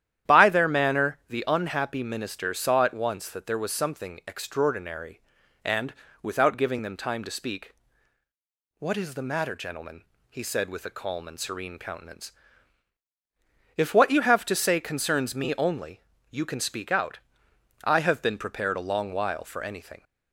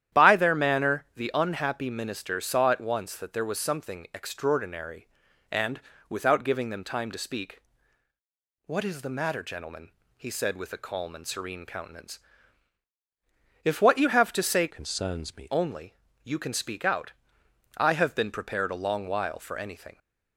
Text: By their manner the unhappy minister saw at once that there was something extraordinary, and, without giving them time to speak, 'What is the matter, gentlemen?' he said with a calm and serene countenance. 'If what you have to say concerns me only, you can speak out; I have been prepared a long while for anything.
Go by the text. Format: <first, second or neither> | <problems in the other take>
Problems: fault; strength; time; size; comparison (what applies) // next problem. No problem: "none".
first | starts louder than the rest; strong; until 1.2 s; 11 dB; strong in the first // changes voice from "concerns" to "me"; from 14.7 to 15.5 s; 0.8 s long